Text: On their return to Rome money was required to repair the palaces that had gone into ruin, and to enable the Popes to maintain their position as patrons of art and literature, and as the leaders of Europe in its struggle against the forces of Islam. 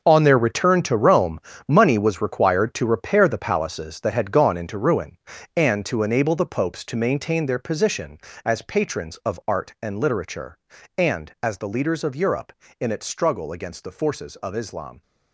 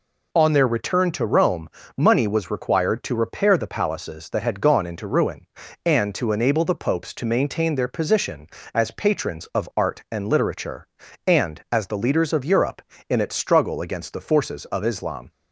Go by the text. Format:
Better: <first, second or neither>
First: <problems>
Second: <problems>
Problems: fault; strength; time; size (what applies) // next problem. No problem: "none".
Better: second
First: gets quieter; strong; throughout; 12.5 dB // pauses between "Rome" and "money"; slight; at 1.3 s; 0.28 s long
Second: pauses between "Rome" and "money"; slight; at 1.6 s; 0.28 s long